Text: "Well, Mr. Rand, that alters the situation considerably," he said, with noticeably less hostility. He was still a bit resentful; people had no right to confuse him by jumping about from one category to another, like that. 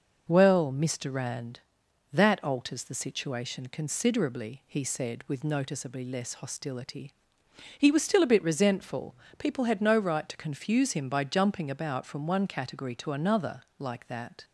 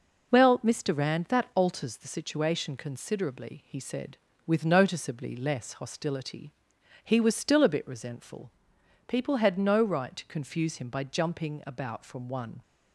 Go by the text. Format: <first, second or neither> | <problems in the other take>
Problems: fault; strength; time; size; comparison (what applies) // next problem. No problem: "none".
first | stops before "category to another like that"; at 12.6 s